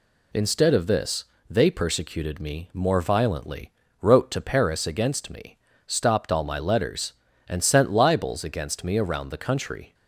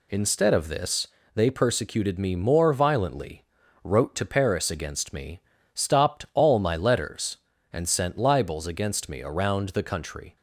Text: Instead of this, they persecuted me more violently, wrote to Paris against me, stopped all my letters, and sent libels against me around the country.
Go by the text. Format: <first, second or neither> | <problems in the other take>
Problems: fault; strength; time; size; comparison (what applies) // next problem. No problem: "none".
neither | none